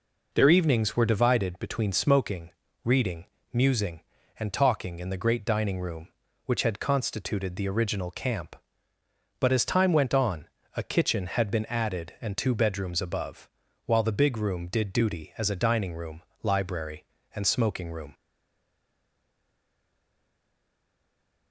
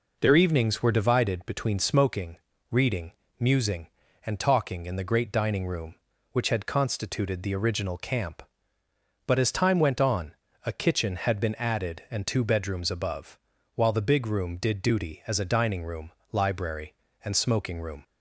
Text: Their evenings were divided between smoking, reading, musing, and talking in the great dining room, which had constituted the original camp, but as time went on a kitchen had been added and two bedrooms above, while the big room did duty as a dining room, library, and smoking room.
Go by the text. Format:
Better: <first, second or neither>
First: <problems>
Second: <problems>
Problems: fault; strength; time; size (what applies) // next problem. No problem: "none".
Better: second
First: pauses between "on" and "a"; slight; at 10.4 s; 0.26 s long // stays silent after the last word; strong; from 18.1 s on; 3.4 s long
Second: pauses between "on" and "a"; slight; at 10.3 s; 0.28 s long